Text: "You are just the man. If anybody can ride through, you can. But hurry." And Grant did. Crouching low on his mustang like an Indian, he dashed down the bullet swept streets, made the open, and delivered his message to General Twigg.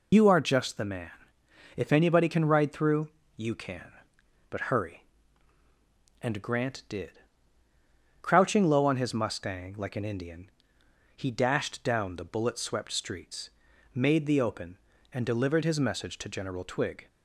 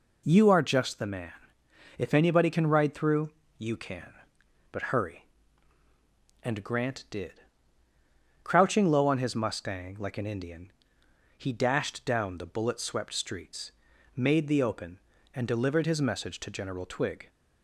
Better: second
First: loses the start of "You"; at 0.1 s; 85 ms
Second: none

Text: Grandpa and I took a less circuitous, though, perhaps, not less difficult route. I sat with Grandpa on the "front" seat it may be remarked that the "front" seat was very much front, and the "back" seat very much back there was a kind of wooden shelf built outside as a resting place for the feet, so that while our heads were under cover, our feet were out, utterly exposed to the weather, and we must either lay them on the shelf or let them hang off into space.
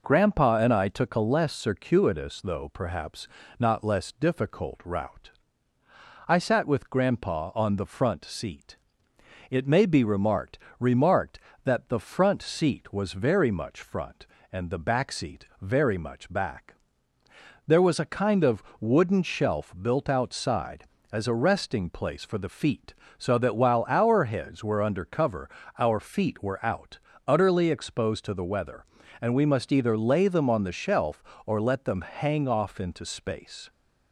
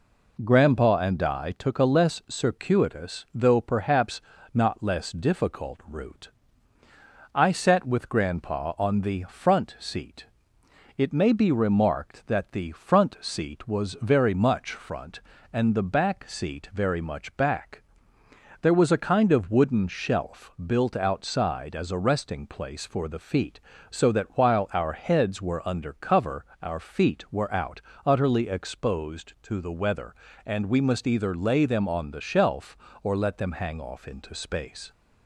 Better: second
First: pauses between "seat" and "it"; noticeable; at 8.7 s; 0.74 s long // says "remarked" twice; at 10.7 s // pauses between "back" and "there"; noticeable; at 16.7 s; 0.92 s long // pauses between "of" and "wooden"; slight; at 18.6 s; 0.18 s long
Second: pauses between "seat" and "it"; noticeable; at 10.2 s; 0.72 s long // pauses between "back" and "there"; noticeable; at 17.8 s; 0.80 s long

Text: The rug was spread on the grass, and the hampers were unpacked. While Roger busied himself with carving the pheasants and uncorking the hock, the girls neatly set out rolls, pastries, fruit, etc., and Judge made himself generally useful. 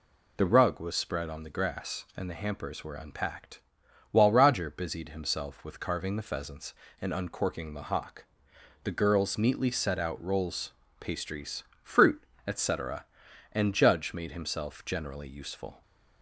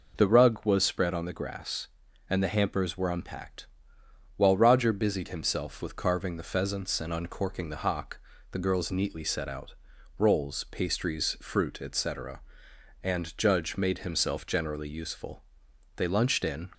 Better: first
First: none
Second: pauses between "out" and "rolls"; at 9.7 s; 0.44 s long // goes on to say "They lunched in"; noticeable; from 15.9 s on; 0.72 s long

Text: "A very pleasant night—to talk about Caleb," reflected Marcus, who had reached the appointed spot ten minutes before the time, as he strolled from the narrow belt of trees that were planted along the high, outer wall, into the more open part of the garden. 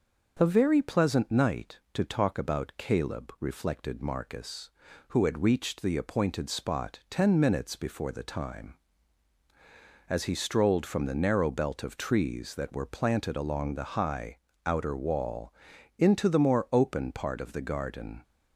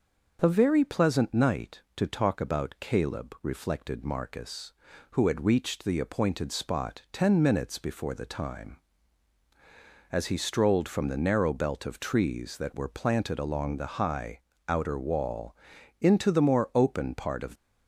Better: first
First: starts louder than the rest; noticeable; until 1.4 s; 6 dB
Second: starts louder than the rest; noticeable; until 1.4 s; 6 dB // stops before "the garden"; at 17.5 s

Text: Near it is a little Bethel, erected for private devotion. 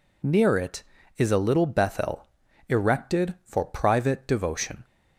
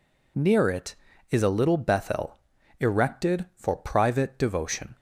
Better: neither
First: none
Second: none

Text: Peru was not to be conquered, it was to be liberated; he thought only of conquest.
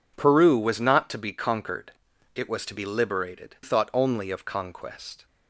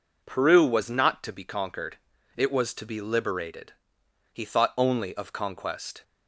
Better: second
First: skips "he"; at 3.5 s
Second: none

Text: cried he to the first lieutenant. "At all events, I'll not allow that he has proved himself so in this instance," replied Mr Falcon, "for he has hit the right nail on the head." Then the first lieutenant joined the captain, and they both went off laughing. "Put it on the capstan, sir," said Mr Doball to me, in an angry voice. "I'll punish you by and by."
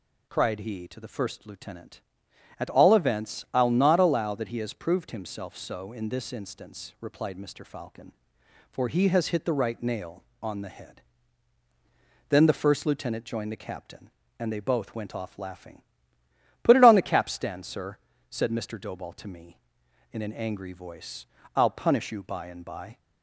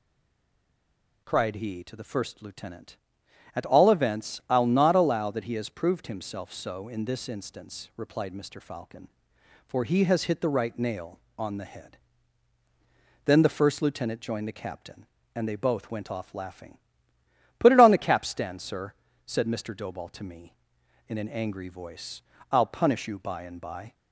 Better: first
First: none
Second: stays silent before the first word; noticeable; until 1.2 s; 1.2 s long

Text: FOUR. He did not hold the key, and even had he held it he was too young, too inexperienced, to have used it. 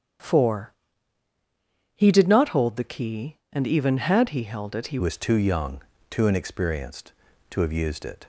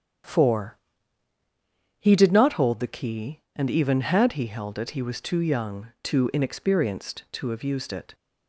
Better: second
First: starts louder than the rest; strong; until 2.4 s; 8.5 dB // changes voice at "was"; from 4.9 s on; 3.3 s long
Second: starts louder than the rest; strong; until 2.4 s; 9 dB

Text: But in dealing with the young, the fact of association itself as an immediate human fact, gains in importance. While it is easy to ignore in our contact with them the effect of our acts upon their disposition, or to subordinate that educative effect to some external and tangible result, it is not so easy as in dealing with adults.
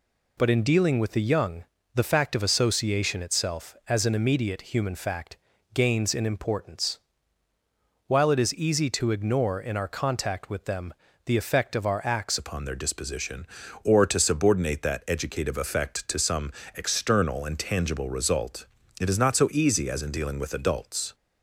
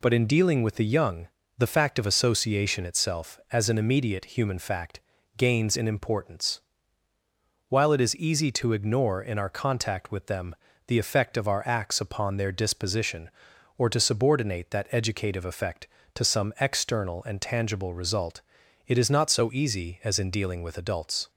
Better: second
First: pauses between "them" and "the"; slight; at 10.9 s; 0.30 s long // changes voice at "upon"; from 12.3 s on; 8.8 s long // pauses between "some" and "external"; slight; at 16.5 s; 0.24 s long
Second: pauses between "them" and "the"; slight; at 10.5 s; 0.30 s long

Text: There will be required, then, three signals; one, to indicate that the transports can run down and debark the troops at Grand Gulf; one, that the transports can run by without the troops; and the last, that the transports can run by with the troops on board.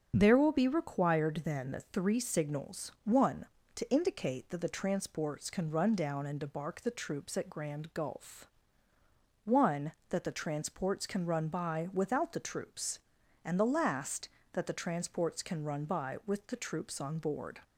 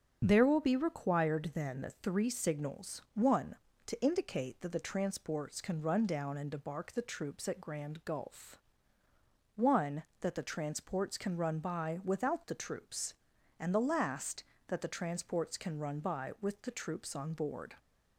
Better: neither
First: starts louder than the rest; until 1.1 s; 7 dB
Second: starts louder than the rest; until 1.2 s; 7 dB

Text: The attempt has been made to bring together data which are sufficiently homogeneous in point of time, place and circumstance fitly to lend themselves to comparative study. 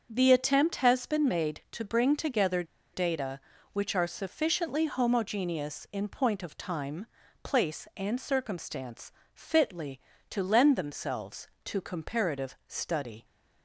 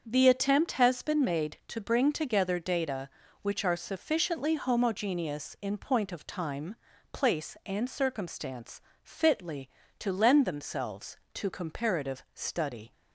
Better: second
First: starts louder than the rest; until 1.1 s; 7 dB // pauses between "together" and "data"; slight; at 2.6 s; 0.29 s long // pauses between "circumstance" and "fitly"; slight; at 9.1 s; 0.22 s long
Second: starts louder than the rest; until 1.0 s; 6.5 dB // pauses between "circumstance" and "fitly"; slight; at 8.7 s; 0.22 s long

